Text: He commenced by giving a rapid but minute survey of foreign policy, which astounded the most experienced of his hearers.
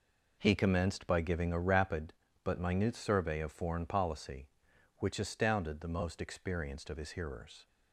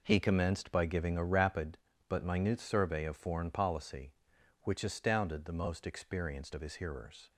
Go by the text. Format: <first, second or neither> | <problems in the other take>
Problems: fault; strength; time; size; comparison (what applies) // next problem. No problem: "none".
neither | none